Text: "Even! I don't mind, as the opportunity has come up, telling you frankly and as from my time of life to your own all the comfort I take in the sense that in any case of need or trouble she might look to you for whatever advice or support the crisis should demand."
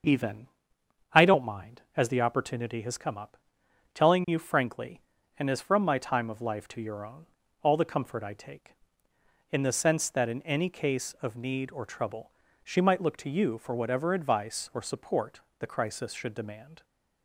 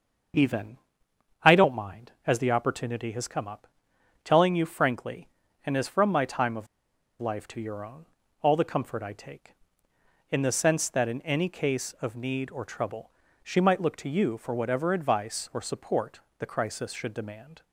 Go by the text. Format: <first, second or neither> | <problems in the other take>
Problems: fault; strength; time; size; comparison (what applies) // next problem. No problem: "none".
first | starts louder than the rest; until 2.0 s; 6.5 dB; also in the first // pauses between "of" and "life"; noticeable; at 6.6 s; 0.52 s long // pauses between "own" and "all"; slight; at 8.0 s; 0.36 s long; slight in the first // pauses between "trouble" and "she"; slight; at 13.1 s; 0.32 s long; slight in the first // pauses between "support" and "the"; slight; at 16.2 s; 0.16 s long; slight in the first